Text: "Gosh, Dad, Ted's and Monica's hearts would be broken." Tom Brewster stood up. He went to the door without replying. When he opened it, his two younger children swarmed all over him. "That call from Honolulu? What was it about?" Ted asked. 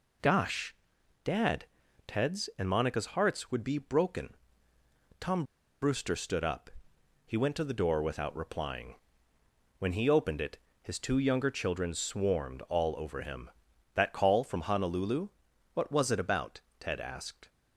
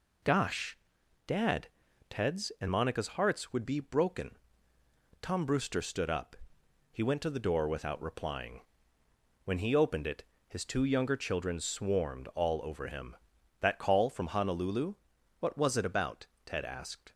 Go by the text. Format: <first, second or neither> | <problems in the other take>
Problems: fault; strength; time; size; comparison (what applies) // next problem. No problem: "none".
second | pauses between "Tom" and "Brewster"; at 5.4 s; 0.38 s long